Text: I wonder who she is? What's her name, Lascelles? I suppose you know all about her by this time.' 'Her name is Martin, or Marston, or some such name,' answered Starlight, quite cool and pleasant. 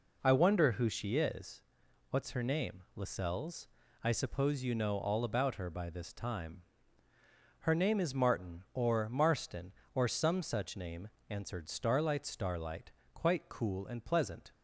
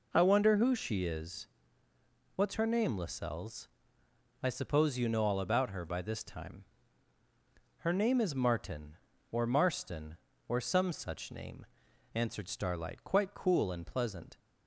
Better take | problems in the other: second | says "Starlight" twice; at 12.2 s

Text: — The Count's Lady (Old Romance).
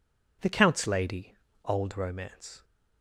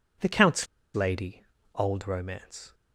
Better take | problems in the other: first | pauses between "Count's" and "Lady"; slight; at 0.6 s; 0.27 s long

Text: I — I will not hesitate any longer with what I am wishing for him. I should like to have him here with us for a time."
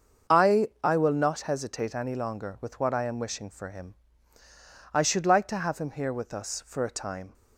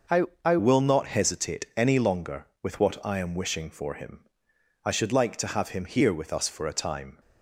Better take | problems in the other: first | starts louder than the rest; noticeable; until 1.3 s; 6 dB; also in the first // changes voice at "will"; from 0.5 s on; 6.6 s long

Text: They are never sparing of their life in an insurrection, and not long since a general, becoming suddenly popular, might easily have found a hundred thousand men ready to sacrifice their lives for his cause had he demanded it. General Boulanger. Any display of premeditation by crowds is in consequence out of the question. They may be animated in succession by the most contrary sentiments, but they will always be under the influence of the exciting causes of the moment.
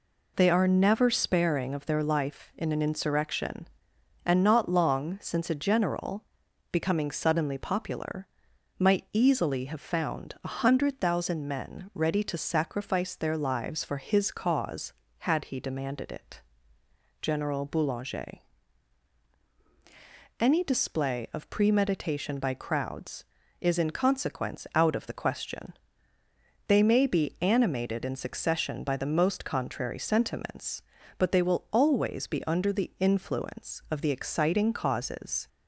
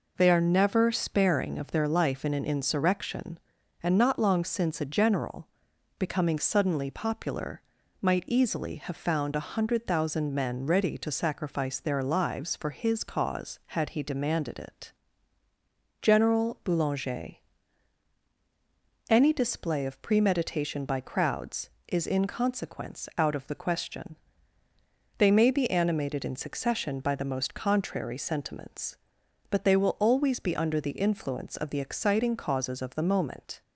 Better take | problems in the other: second | stops before "of the moment"; at 35.4 s

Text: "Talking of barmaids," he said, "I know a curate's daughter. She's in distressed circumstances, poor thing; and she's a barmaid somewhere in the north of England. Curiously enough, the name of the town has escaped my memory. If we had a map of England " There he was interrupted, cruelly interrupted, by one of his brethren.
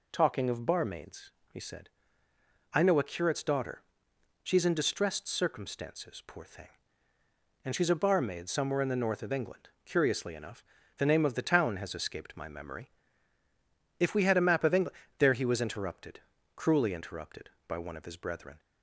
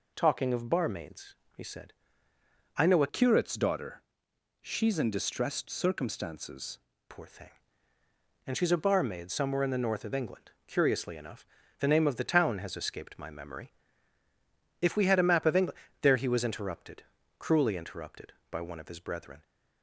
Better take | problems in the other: first | changes voice from "curate's" to "circumstances"; from 3.0 to 6.7 s; 3.7 s long

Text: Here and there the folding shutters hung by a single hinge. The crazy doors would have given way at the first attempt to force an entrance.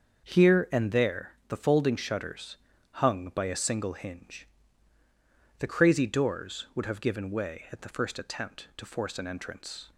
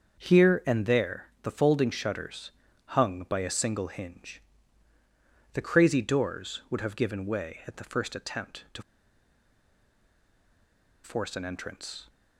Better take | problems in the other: first | starts louder than the rest; until 1.2 s; 6.5 dB; also in the first // pauses between "there" and "the"; slight; at 1.2 s; 0.16 s long; slight in the first // pauses between "shutters" and "hung"; slight; at 2.4 s; 0.36 s long; slight in the first // pauses between "to" and "force"; strong; at 8.8 s; 2.2 s long

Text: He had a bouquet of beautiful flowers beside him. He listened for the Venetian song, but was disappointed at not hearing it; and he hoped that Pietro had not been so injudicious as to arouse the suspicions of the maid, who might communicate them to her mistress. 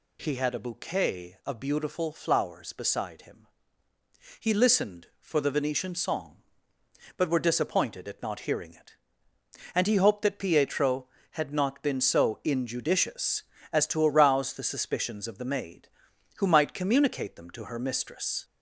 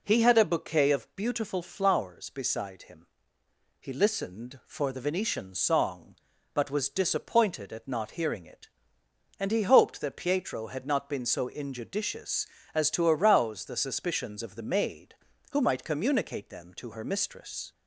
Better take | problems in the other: second | says "were" for "was"; at 7.3 s

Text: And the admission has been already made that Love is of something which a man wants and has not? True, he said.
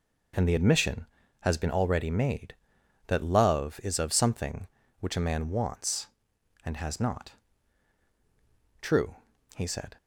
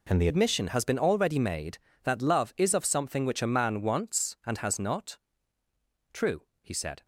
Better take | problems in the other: first | changes voice at "admission"; from 0.2 s on; 6.8 s long

